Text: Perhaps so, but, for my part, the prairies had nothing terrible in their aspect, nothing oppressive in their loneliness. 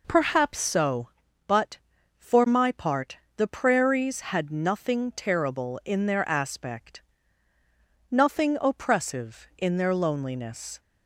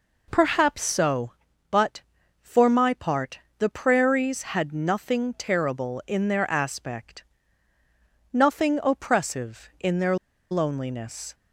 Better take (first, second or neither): first